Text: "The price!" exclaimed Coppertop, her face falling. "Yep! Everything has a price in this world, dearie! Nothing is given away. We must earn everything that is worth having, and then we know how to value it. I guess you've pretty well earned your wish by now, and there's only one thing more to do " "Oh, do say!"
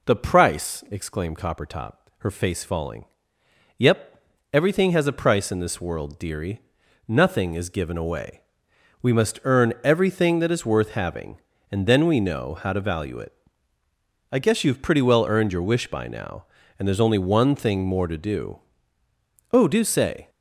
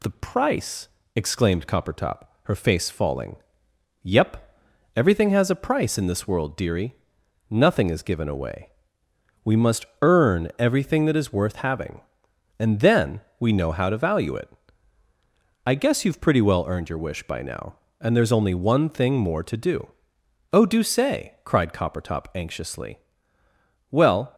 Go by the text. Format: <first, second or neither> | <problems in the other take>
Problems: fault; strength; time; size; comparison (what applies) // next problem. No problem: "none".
first | pauses between "must" and "earn"; slight; at 9.8 s; 0.16 s long // pauses between "then" and "we"; slight; at 13.2 s; 0.18 s long // goes on to say "cried Coppertop anxiously Well"; strong; from 21.4 s on; 2.9 s long